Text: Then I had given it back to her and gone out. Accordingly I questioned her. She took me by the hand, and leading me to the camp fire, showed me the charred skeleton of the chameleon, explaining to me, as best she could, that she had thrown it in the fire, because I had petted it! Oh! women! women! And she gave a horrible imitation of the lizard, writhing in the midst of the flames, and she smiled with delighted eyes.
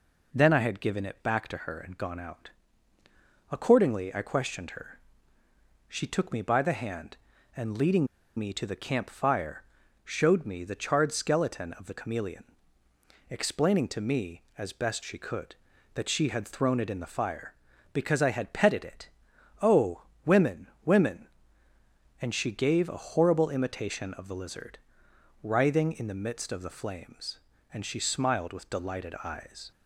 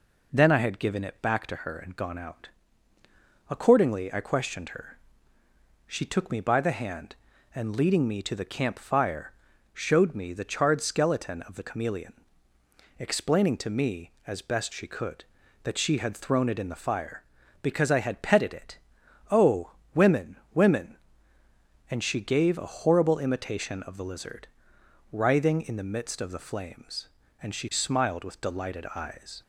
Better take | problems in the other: second | pauses between "leading" and "me"; slight; at 8.0 s; 0.29 s long

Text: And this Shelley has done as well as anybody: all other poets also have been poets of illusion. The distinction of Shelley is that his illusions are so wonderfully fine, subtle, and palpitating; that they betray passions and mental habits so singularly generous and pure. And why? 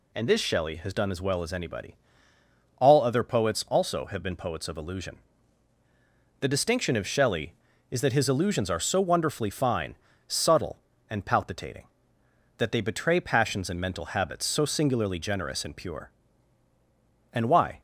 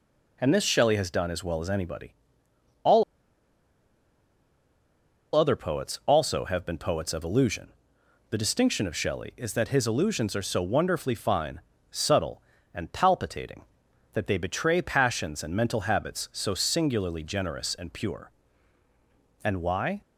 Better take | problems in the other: first | pauses between "all" and "other"; strong; at 3.0 s; 2.3 s long

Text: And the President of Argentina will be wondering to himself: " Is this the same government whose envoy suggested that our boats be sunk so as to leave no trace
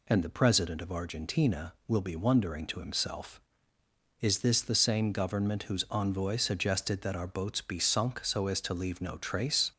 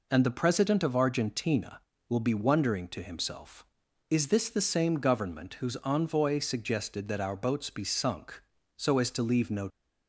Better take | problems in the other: first | stops before "trace"; at 9.7 s

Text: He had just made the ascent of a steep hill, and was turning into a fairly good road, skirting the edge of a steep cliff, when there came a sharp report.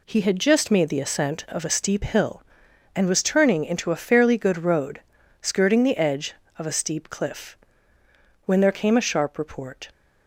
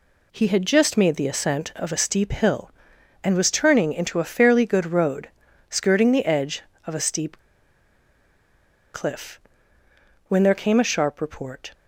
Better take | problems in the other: first | pauses between "steep" and "cliff"; strong; at 7.3 s; 1.5 s long

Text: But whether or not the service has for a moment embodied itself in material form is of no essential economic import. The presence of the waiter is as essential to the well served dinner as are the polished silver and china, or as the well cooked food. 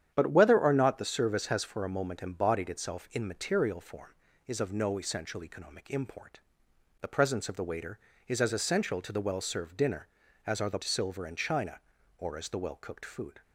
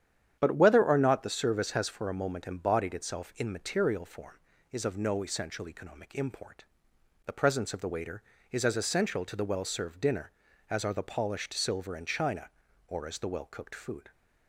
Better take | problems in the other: second | starts louder than the rest; strong; until 1.1 s; 9.5 dB; strong in the second // skips "polished"; at 10.8 s

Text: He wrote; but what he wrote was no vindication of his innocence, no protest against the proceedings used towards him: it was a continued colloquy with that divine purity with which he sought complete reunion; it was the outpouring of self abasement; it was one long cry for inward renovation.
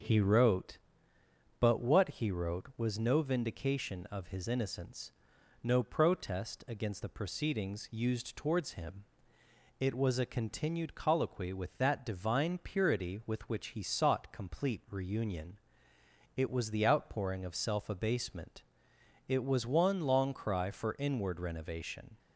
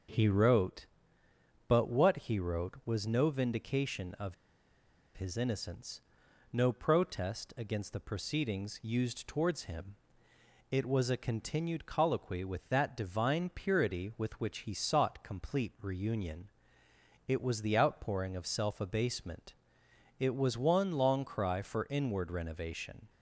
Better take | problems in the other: first | starts louder than the rest; until 1.9 s; 6 dB; also in the first // pauses between "of" and "his"; noticeable; at 4.3 s; 0.82 s long

